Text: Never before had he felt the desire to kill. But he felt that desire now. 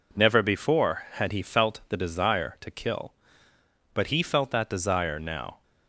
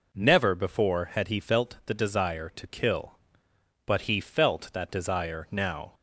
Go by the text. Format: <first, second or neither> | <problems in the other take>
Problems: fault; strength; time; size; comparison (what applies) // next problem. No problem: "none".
neither | none